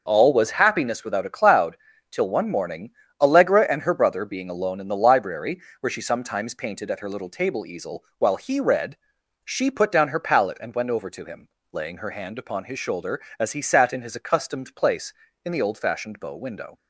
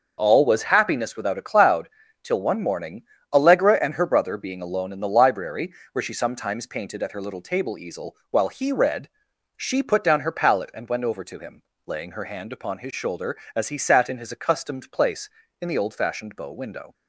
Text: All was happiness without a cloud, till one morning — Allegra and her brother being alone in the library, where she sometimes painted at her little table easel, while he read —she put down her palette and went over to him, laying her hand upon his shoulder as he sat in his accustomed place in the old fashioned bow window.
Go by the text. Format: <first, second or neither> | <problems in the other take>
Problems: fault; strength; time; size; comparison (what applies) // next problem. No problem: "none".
neither | none